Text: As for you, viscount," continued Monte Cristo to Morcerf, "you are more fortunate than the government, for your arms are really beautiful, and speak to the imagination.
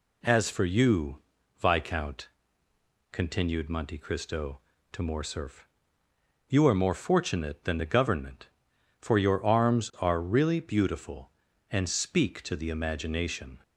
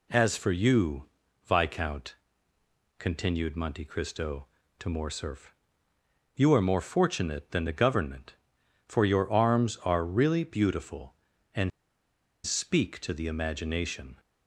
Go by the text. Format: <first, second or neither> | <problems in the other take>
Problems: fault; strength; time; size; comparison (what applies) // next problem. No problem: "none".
first | pauses between "and" and "speak"; noticeable; at 11.7 s; 0.75 s long